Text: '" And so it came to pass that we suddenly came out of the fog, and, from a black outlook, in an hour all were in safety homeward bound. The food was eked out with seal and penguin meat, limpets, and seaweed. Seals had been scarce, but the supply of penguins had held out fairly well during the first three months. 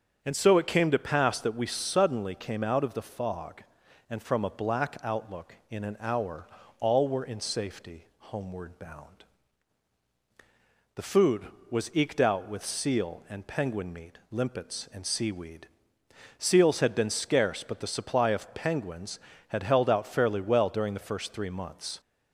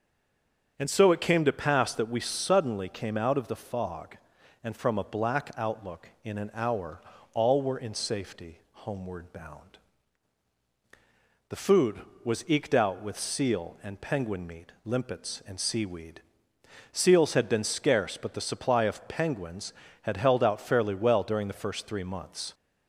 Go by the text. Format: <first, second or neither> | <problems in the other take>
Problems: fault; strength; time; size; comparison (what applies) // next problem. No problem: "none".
first | stays silent before the first word; slight; until 0.7 s; 0.7 s long // starts louder than the rest; strong; until 1.7 s; 7.5 dB; strong in the first // pauses between "hour" and "all"; slight; at 6.9 s; 0.32 s long; slight in the first